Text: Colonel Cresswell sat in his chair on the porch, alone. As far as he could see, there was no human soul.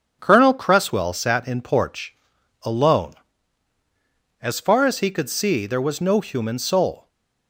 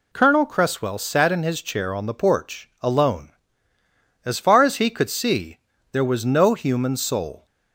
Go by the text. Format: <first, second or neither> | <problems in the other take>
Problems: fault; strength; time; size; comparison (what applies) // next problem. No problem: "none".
second | starts louder than the rest; strong; until 1.2 s; 8 dB // skips "his chair on the"; at 1.6 s